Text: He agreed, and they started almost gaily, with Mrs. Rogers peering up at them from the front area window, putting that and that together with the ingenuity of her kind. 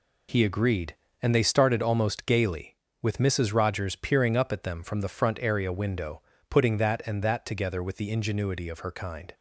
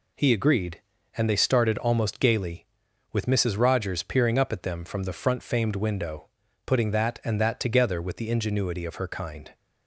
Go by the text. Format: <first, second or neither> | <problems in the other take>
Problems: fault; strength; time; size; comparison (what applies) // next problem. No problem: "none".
first | says "famed" for "area"; at 5.4 s